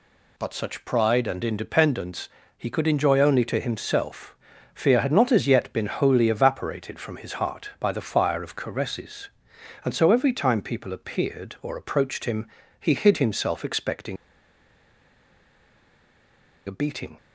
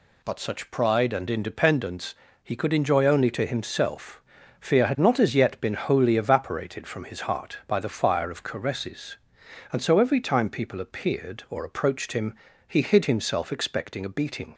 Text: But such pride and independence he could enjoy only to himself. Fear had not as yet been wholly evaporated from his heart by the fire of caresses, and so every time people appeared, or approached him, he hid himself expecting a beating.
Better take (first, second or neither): second